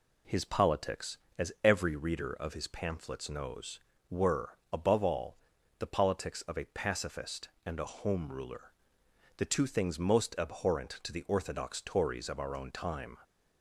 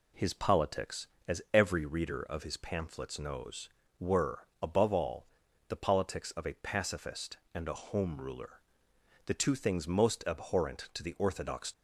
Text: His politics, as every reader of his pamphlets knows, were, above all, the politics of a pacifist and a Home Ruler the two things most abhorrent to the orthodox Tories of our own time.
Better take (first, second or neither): first